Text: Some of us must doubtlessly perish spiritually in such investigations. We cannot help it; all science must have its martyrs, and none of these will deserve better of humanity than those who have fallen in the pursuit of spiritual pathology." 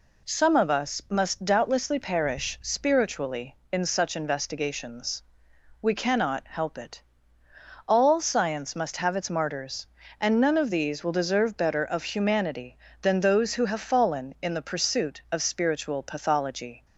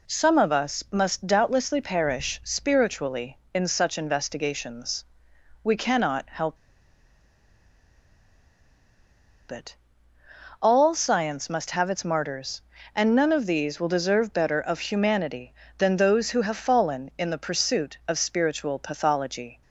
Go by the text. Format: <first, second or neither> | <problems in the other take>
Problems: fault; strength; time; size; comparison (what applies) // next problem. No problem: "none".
first | pauses between "help" and "it"; strong; at 6.5 s; 2.9 s long